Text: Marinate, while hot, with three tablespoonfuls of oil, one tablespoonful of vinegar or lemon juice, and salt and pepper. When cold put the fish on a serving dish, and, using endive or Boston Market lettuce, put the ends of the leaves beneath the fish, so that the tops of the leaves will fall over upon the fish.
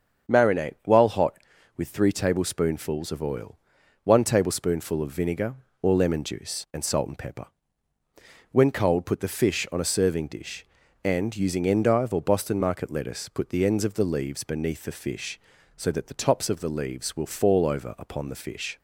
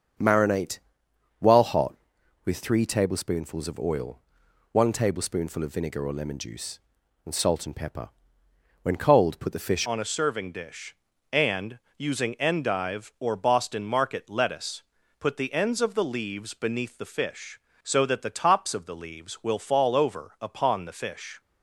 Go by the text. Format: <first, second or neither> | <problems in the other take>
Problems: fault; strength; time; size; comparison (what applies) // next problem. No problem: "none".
first | starts louder than the rest; strong; until 1.8 s; 7 dB; also in the first // changes voice at "on"; from 9.8 s on; 11.5 s long